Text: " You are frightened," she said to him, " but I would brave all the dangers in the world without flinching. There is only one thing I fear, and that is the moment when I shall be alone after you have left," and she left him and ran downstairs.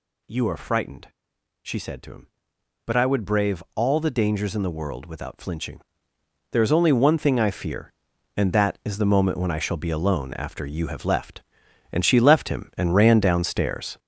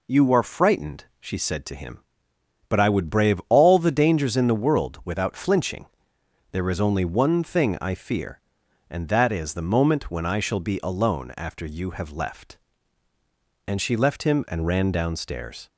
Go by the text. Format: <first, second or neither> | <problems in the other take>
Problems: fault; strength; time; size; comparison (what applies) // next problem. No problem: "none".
second | gets louder; strong; throughout; 12 dB